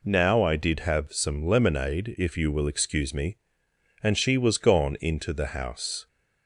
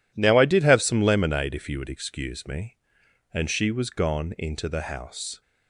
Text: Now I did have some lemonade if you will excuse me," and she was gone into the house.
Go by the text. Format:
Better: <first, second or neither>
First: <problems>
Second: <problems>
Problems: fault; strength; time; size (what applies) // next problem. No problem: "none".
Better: first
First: none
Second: says "would" for "will"; at 1.7 s